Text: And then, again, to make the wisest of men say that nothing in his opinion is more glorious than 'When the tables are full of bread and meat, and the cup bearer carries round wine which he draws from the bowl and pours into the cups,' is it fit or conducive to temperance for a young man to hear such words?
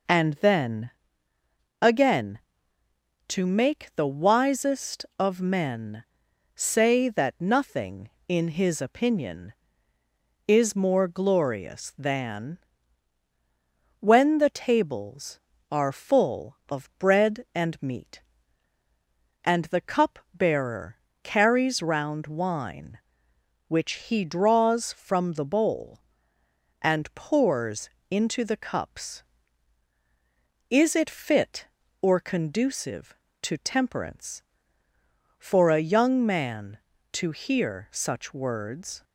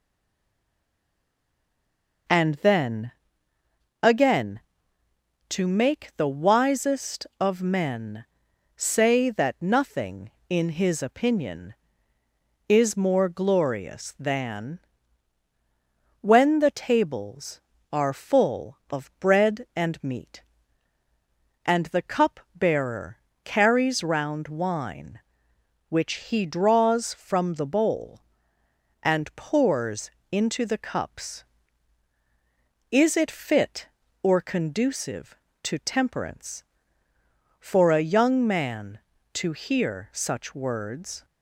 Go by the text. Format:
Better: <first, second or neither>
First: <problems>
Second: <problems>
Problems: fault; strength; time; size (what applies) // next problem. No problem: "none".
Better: first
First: pauses between "men" and "say"; noticeable; at 6.0 s; 0.52 s long // pauses between "than" and "When"; strong; at 12.5 s; 1.4 s long // pauses between "bearer" and "carries"; slight; at 20.9 s; 0.26 s long // pauses between "pours" and "into"; slight; at 27.8 s; 0.22 s long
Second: stays silent before the first word; until 2.2 s; 2.2 s long // pauses between "men" and "say"; noticeable; at 8.2 s; 0.52 s long // pauses between "than" and "When"; strong; at 14.8 s; 1.4 s long // pauses between "bearer" and "carries"; slight; at 23.1 s; 0.26 s long // pauses between "pours" and "into"; slight; at 30.1 s; 0.22 s long